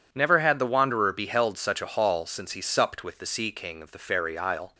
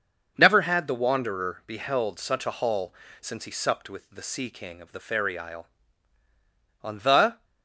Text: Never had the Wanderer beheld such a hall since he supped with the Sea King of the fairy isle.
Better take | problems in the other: first | starts louder than the rest; until 1.3 s; 6 dB // pauses between "hall" and "since"; slight; at 2.9 s; 0.28 s long // goes on to say "On the"; noticeable; from 6.8 s on; 0.62 s long

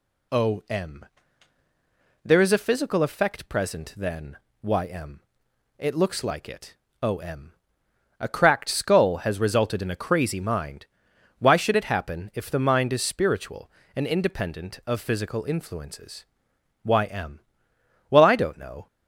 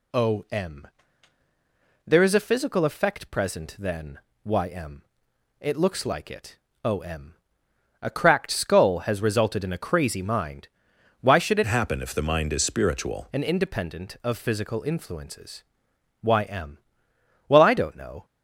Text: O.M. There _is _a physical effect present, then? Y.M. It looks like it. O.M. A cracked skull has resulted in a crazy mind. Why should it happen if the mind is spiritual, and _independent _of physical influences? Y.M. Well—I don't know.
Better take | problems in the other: first | changes voice from "happen" to "spiritual"; from 11.6 to 13.2 s; 1.6 s long

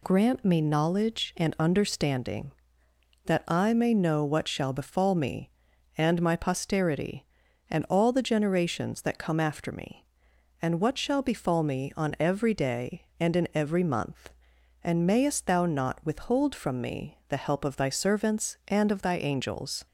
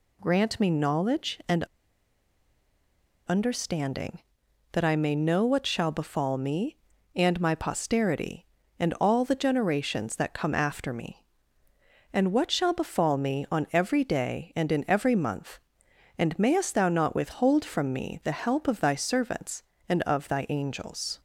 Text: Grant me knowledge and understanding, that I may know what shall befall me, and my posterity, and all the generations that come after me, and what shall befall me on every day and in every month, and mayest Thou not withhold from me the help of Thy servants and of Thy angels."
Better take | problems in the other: first | pauses between "and" and "understanding"; strong; at 1.6 s; 1.6 s long

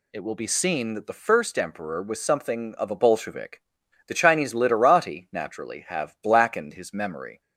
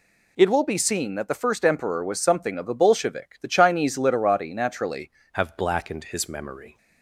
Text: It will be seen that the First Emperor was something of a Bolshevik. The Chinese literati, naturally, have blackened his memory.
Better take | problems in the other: first | changes voice at "have"; from 5.3 s on; 1.4 s long

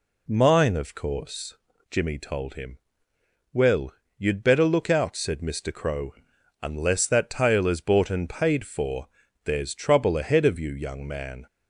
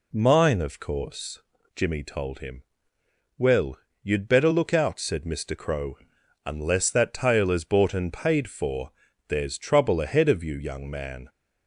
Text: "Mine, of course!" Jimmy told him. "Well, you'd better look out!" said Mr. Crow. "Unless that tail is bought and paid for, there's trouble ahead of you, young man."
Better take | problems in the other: neither | none

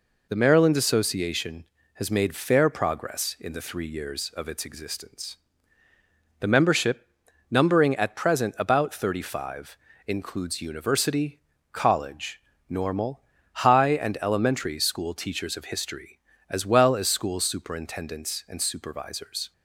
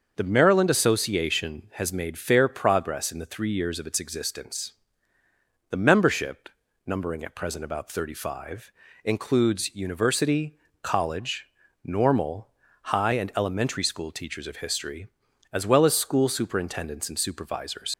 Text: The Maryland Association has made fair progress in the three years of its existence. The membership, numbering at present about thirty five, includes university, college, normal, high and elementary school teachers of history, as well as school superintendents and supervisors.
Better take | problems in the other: first | starts louder than the rest; until 1.1 s; 6.5 dB // leaves "supervisors" unfinished; at 17.9 s; 65 ms

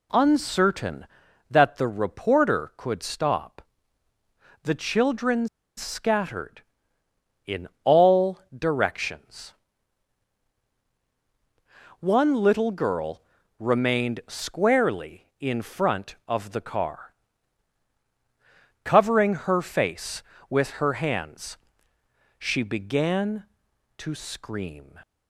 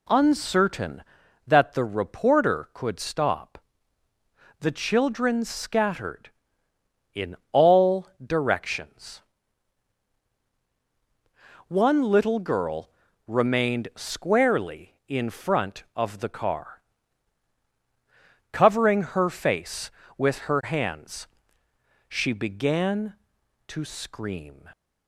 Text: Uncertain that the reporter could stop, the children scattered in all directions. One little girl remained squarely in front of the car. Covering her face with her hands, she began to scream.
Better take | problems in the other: second | pauses between "children" and "scattered"; slight; at 5.4 s; 0.30 s long // pauses between "in" and "all"; slight; at 7.6 s; 0.16 s long; slight in the second // pauses between "all" and "directions"; slight; at 8.3 s; 0.18 s long; slight in the second // pauses between "girl" and "remained"; at 13.2 s; 0.38 s long; also in the second

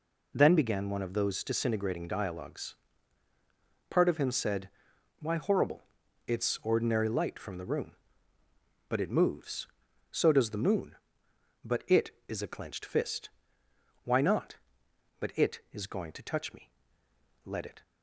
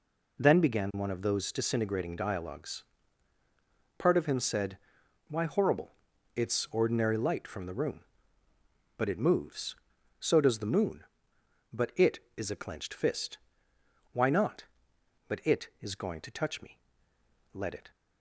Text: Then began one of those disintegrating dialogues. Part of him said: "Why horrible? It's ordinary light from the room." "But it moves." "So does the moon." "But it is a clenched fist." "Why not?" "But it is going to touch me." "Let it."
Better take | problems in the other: neither | none

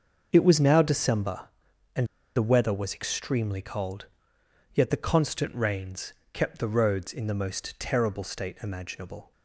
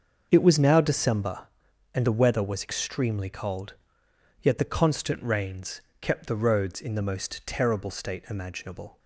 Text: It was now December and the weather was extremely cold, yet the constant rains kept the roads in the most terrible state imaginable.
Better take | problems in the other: second | starts louder than the rest; until 1.3 s; 6.5 dB; also in the second // pauses between "and" and "the"; slight; at 2.0 s; 0.29 s long // pauses between "rains" and "kept"; slight; at 6.1 s; 0.22 s long; slight in the second

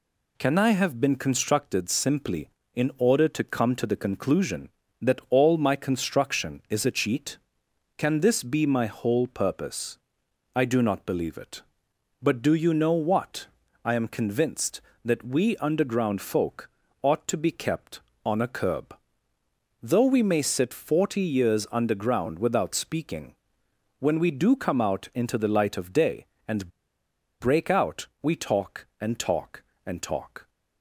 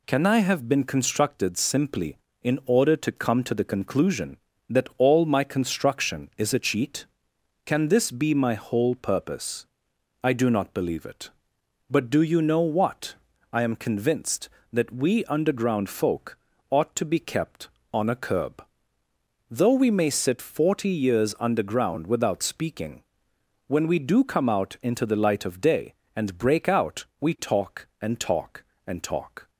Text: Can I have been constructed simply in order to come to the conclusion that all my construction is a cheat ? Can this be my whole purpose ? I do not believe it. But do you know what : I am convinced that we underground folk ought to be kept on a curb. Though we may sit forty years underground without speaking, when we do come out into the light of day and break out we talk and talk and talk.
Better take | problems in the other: second | pauses between "folk" and "ought"; slight; at 16.6 s; 0.32 s long; slight in the second // pauses between "and" and "break"; noticeable; at 26.6 s; 0.71 s long // pauses between "out" and "we"; slight; at 28.0 s; 0.16 s long; slight in the second

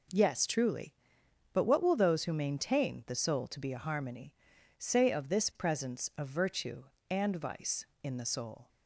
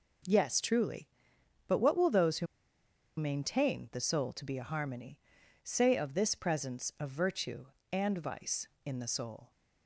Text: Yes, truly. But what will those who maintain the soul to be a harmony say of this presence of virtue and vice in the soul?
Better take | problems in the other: first | pauses between "who" and "maintain"; noticeable; at 2.4 s; 0.72 s long // pauses between "harmony" and "say"; at 5.1 s; 0.44 s long; also in the first

